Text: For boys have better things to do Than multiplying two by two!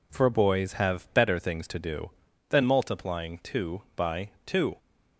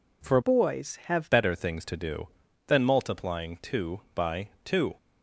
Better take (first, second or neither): first